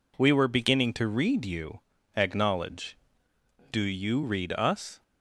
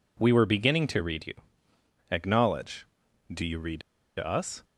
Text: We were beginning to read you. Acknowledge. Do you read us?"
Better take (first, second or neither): first